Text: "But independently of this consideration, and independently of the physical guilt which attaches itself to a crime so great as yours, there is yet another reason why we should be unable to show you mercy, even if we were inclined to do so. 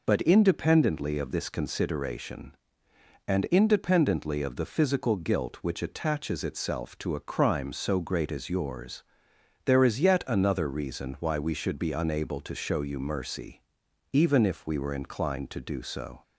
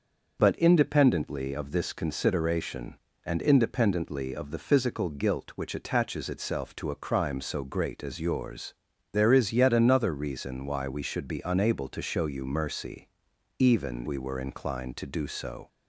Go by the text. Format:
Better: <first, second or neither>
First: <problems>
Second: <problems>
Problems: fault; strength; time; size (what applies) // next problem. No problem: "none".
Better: first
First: none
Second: starts louder than the rest; until 1.4 s; 6 dB // skips "if"; at 14.0 s